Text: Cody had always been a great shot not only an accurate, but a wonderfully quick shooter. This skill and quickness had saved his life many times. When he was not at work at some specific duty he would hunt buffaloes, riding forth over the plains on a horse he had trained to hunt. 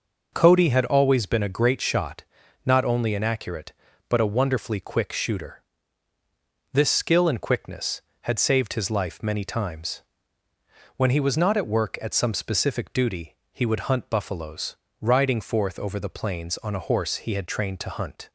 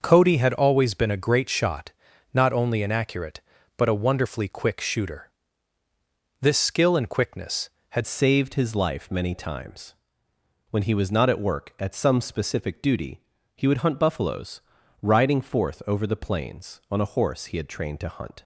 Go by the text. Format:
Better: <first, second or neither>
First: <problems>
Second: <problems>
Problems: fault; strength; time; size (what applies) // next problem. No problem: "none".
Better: first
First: pauses between "shot" and "not"; at 2.2 s; 0.42 s long // pauses between "duty" and "he"; slight; at 13.3 s; 0.16 s long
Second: starts louder than the rest; noticeable; until 1.0 s; 6 dB // pauses between "shot" and "not"; at 1.9 s; 0.42 s long // changes voice at "saved"; from 8.0 s on; 10.4 s long // pauses between "duty" and "he"; slight; at 13.2 s; 0.34 s long